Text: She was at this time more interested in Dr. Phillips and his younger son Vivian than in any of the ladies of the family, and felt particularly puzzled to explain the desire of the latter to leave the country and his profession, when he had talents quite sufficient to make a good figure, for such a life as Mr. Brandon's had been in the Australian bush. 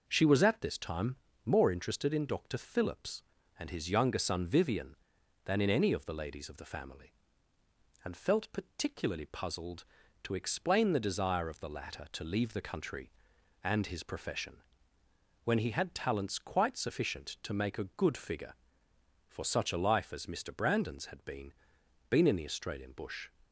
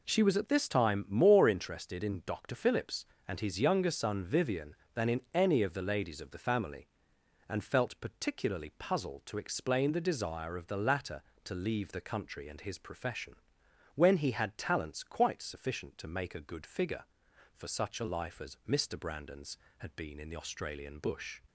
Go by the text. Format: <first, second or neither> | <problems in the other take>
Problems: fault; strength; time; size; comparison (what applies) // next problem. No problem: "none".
second | pauses between "time" and "more"; slight; at 1.1 s; 0.28 s long // says "been" twice; at 22.0 s